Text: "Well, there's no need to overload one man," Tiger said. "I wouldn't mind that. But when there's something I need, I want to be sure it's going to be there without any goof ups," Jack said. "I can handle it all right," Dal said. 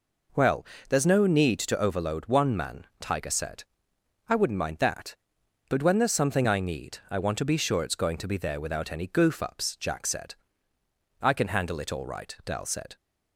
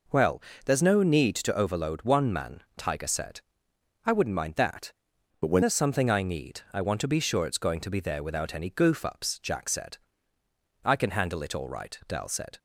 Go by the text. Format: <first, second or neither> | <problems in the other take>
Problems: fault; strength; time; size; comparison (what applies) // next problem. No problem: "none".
first | changes voice from "But" to "when"; from 5.4 to 5.6 s; 0.2 s long